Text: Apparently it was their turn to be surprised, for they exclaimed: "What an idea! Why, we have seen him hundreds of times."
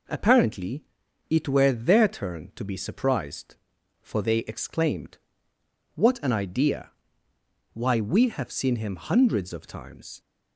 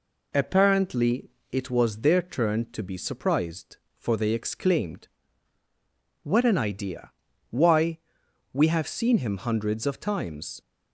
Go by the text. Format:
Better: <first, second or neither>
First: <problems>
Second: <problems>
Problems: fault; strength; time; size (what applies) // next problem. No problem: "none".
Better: second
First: pauses between "Apparently" and "it"; noticeable; at 0.8 s; 0.46 s long // says "were" for "was"; at 1.4 s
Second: pauses between "Apparently" and "it"; slight; at 1.3 s; 0.20 s long